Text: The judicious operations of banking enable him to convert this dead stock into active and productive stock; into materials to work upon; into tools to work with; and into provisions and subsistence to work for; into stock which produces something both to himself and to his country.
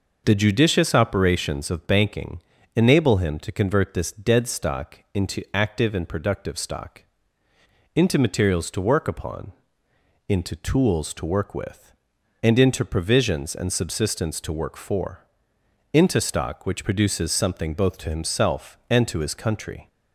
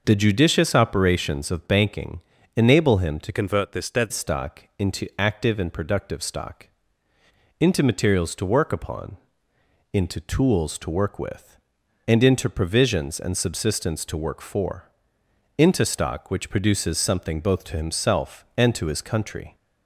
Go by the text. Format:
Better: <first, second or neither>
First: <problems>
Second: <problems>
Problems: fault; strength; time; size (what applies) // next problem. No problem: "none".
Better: first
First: pauses between "banking" and "enable"; slight; at 2.3 s; 0.34 s long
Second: pauses between "banking" and "enable"; slight; at 2.2 s; 0.34 s long // changes voice from "convert" to "dead"; from 3.3 to 4.1 s; 0.8 s long